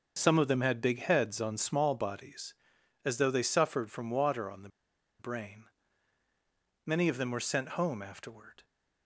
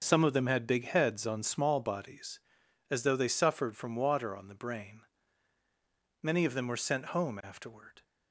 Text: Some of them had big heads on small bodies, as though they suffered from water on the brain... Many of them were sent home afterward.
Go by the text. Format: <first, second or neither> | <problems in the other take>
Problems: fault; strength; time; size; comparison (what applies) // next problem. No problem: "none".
second | starts louder than the rest; until 1.2 s; 6.5 dB; also in the second // pauses between "the" and "brain"; noticeable; at 4.6 s; 0.50 s long